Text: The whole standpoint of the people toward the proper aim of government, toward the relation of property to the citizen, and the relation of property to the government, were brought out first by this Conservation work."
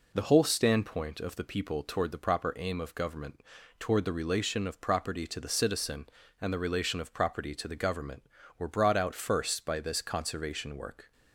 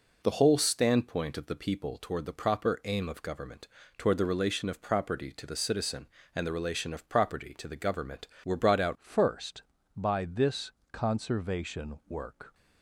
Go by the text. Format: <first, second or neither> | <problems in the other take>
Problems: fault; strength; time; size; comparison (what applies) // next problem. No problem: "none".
first | changes voice at "first"; from 8.9 s on; 3.6 s long // pauses between "this" and "Conservation"; slight; at 10.7 s; 0.20 s long